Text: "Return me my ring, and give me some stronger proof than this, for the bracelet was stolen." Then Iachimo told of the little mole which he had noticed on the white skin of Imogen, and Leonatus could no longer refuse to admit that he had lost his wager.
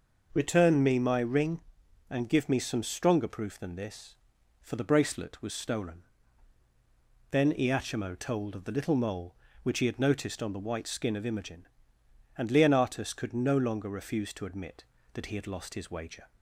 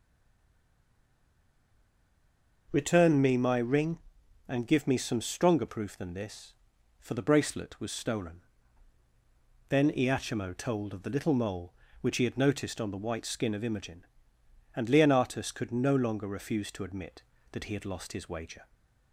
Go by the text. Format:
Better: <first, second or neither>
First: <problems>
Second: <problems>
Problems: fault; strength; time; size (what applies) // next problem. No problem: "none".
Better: first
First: none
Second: stays silent before the first word; strong; until 2.6 s; 2.6 s long